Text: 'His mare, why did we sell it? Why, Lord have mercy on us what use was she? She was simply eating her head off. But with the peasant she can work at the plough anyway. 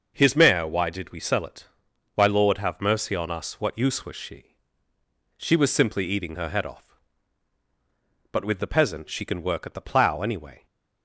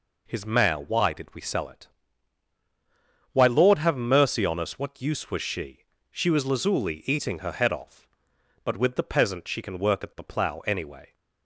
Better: first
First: none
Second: says "lazuli" for "simply"; at 6.4 s

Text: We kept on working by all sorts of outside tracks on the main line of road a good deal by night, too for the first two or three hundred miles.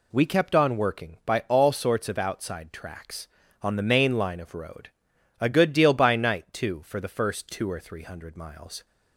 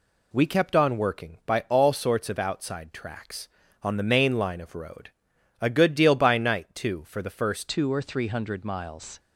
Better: first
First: pauses between "road" and "a"; noticeable; at 4.8 s; 0.50 s long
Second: pauses between "road" and "a"; noticeable; at 5.0 s; 0.50 s long // changes voice at "two"; from 7.6 s on; 1.5 s long

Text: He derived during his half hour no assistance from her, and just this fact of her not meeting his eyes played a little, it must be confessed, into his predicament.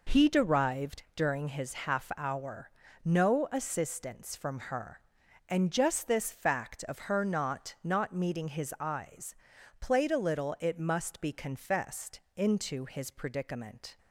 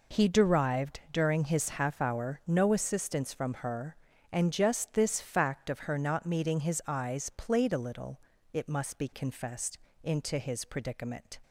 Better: second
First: pauses between "hour" and "no"; slight; at 2.7 s; 0.32 s long // says "not" twice; at 7.8 s // pauses between "eyes" and "played"; noticeable; at 9.3 s; 0.46 s long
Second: none

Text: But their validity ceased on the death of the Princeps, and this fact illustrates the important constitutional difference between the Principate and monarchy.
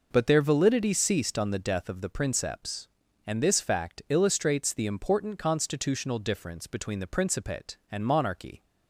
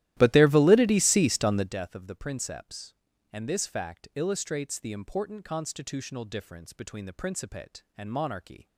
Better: first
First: none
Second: starts louder than the rest; strong; until 1.7 s; 14.5 dB

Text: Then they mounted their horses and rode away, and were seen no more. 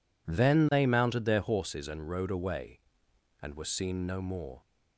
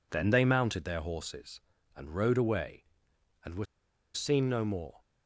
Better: first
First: none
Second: pauses between "were" and "seen"; noticeable; at 3.6 s; 0.48 s long

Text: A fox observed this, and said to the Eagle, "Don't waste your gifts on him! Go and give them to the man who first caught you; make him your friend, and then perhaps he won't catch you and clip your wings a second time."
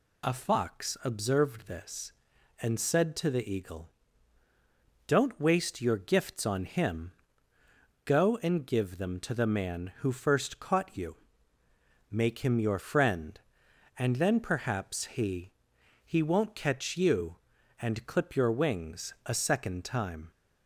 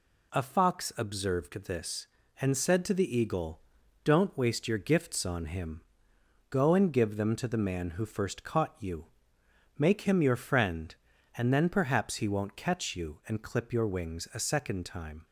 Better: second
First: says "he" twice; at 16.0 s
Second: none

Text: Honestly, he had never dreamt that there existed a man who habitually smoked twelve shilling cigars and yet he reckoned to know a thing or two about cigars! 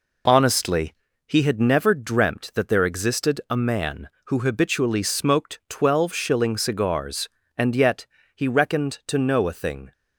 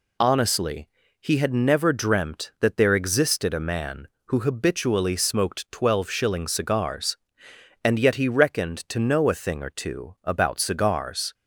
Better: second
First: pauses between "yet" and "he"; slight; at 8.0 s; 0.28 s long // stops before "or two about cigars"; at 9.9 s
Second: none

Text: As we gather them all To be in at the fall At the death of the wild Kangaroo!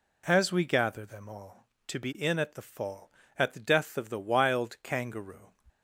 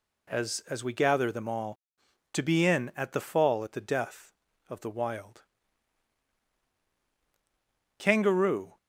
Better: first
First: none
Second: says "As" twice; at 0.6 s // pauses between "wild" and "Kangaroo"; strong; at 5.4 s; 2.5 s long

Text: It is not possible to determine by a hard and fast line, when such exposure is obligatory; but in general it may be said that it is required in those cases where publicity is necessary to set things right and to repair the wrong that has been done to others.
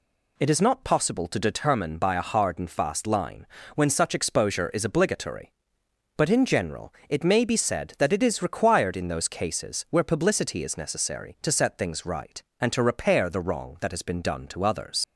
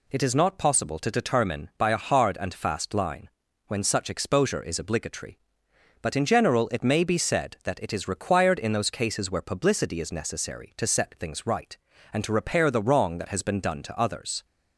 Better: second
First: leaves "others" unfinished; at 15.0 s; 95 ms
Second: none

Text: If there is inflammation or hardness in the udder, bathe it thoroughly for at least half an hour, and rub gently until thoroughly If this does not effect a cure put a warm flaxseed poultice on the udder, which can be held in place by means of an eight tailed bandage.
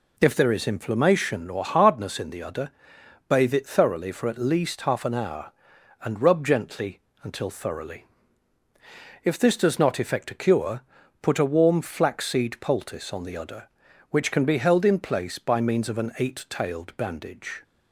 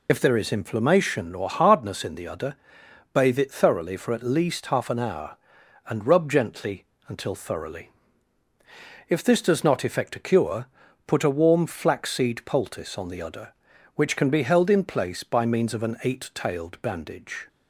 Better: first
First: pauses between "gently" and "until"; slight; at 7.0 s; 0.22 s long // pauses between "thoroughly" and "If"; at 8.0 s; 1.2 s long // pauses between "cure" and "put"; at 10.8 s; 0.40 s long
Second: loses the start of "If"; at 0.0 s; 60 ms // pauses between "gently" and "until"; slight; at 6.8 s; 0.22 s long // pauses between "thoroughly" and "If"; at 7.8 s; 1.2 s long // pauses between "cure" and "put"; at 10.6 s; 0.40 s long

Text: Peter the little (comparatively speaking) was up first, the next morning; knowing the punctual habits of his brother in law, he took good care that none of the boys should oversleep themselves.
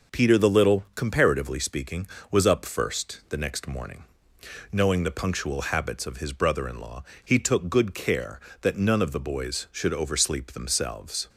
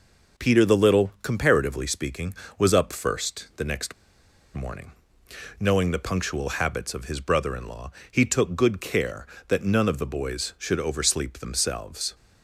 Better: first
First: none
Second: pauses between "next" and "morning"; noticeable; at 3.9 s; 0.61 s long

